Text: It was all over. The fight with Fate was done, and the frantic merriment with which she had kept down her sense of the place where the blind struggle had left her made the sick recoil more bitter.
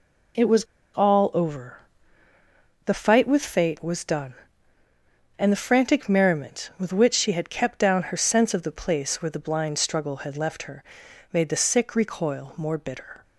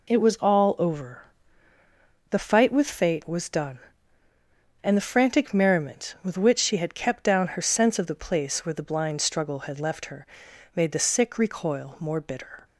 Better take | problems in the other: second | pauses between "was" and "all"; slight; at 0.6 s; 0.29 s long // pauses between "her" and "made"; noticeable; at 10.8 s; 0.52 s long; noticeable in the second

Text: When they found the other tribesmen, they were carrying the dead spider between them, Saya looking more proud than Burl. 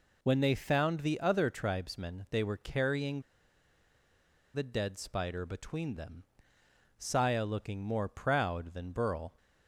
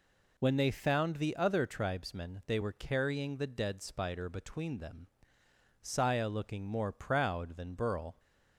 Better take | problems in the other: second | pauses between "carrying" and "the"; strong; at 3.2 s; 1.3 s long

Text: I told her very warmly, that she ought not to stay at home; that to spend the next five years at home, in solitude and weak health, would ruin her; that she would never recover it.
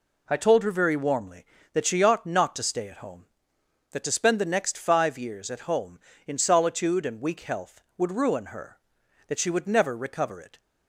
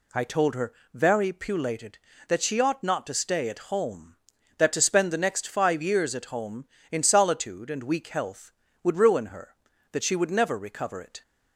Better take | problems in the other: first | pauses between "her" and "very"; slight; at 0.7 s; 0.20 s long // says "pulated" for "warmly"; at 1.3 s

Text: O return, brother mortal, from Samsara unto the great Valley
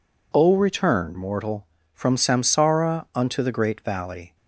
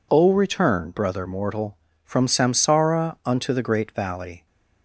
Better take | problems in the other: second | skips "brother"; at 1.1 s

